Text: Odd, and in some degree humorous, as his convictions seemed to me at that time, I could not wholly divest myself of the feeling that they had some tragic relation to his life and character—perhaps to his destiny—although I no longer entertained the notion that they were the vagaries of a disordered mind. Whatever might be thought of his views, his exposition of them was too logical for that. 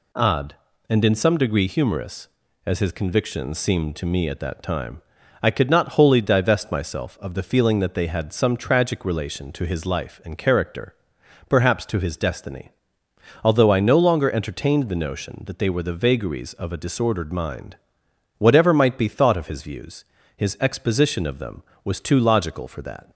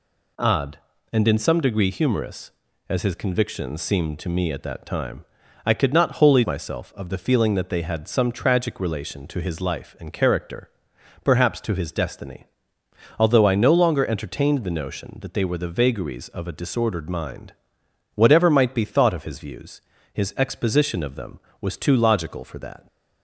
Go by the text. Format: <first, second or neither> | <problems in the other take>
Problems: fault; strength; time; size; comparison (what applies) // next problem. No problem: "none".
first | skips "divest"; at 6.4 s